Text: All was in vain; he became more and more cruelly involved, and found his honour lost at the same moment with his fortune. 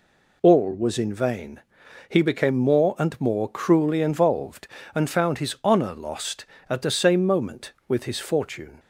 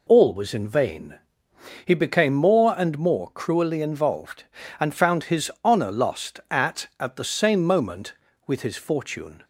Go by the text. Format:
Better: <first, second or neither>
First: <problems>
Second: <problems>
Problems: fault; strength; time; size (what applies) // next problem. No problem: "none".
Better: first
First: none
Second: says "at" twice; at 6.9 s